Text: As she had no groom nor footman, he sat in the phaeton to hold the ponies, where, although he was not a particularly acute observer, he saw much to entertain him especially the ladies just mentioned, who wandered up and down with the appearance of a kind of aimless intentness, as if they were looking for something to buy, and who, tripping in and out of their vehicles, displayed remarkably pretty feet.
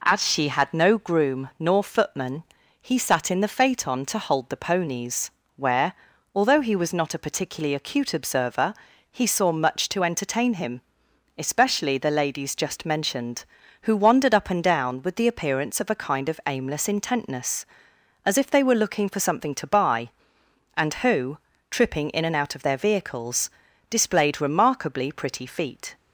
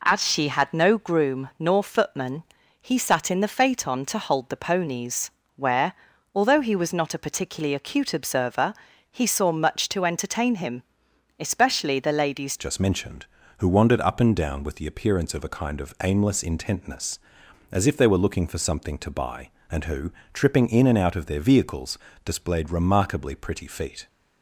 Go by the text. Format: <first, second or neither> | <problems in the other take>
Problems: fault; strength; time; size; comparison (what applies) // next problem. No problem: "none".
first | pauses between "him" and "especially"; noticeable; at 10.8 s; 0.58 s long; noticeable in the first // changes voice at "just"; from 12.5 s on; 11.5 s long